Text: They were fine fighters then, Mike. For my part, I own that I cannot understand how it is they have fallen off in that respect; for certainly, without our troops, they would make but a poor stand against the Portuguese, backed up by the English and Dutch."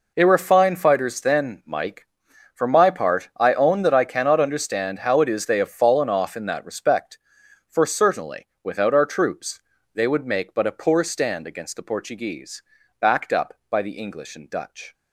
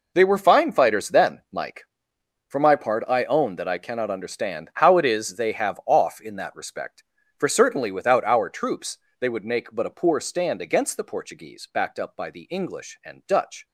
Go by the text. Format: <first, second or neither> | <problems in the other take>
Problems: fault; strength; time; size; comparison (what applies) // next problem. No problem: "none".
first | skips "fallen"; at 5.8 s